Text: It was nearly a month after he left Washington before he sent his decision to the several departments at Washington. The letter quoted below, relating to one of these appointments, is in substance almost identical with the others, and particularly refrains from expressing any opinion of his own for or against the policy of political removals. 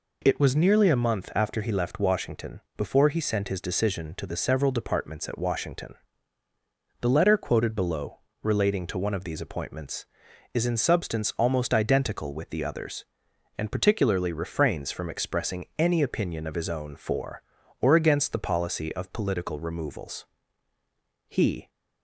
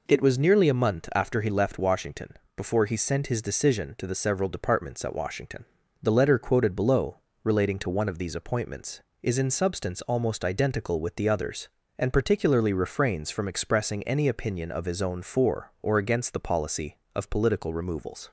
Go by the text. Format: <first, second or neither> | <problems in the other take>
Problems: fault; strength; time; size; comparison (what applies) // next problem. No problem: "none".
second | pauses between "Washington" and "before"; slight; at 2.6 s; 0.16 s long; slight in the second // goes on to say "He"; slight; from 21.2 s on; 0.42 s long